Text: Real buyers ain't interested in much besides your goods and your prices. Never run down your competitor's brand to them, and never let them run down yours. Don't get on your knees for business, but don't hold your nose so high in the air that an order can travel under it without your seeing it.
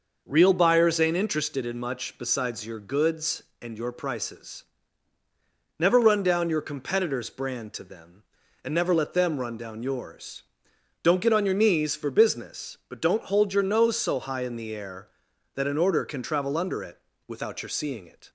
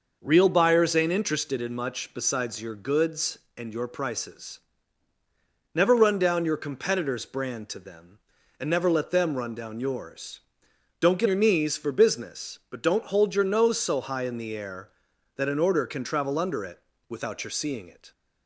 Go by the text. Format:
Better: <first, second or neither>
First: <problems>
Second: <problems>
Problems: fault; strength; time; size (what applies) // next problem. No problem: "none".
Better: first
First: pauses between "it" and "without"; slight; at 16.9 s; 0.28 s long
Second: skips "on"; at 11.2 s // pauses between "it" and "without"; slight; at 16.7 s; 0.28 s long